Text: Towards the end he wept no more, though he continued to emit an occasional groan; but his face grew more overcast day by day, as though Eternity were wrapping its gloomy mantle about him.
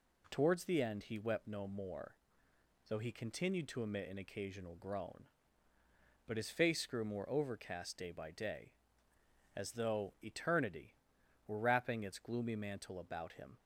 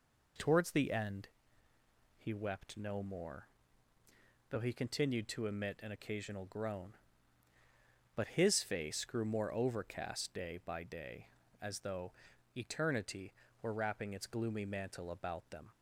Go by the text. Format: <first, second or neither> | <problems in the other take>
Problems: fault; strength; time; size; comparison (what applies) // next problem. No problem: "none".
first | pauses between "end" and "he"; noticeable; at 1.2 s; 0.88 s long // pauses between "though" and "Eternity"; at 12.1 s; 0.42 s long // says "them" for "him"; at 15.4 s